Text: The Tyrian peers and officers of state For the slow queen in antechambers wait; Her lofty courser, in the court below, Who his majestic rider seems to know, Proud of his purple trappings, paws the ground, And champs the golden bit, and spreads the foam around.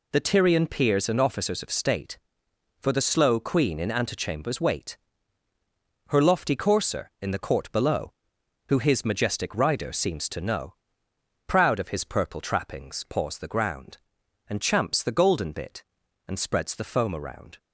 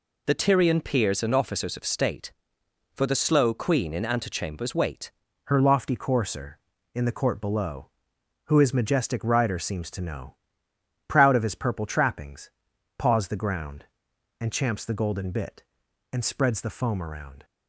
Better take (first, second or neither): first